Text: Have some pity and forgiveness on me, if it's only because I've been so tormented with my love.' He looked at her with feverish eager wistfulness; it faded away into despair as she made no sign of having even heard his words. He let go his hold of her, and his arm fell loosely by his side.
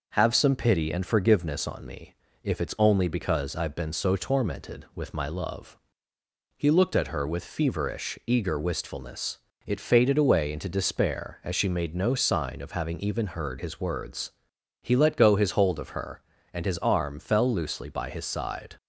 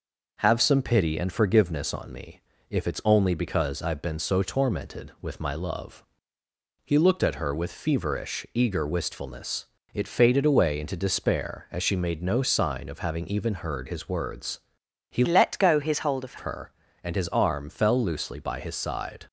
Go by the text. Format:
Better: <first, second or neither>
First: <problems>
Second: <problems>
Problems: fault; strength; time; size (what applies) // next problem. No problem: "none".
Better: first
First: none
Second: changes voice from "let" to "of"; from 15.2 to 16.3 s; 1.1 s long